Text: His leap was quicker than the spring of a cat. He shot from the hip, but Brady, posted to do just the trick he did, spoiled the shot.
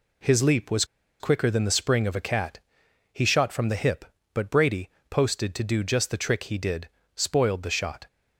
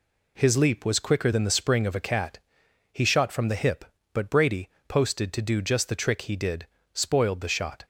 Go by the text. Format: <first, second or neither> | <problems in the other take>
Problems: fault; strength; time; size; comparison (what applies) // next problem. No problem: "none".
second | pauses between "was" and "quicker"; slight; at 0.8 s; 0.36 s long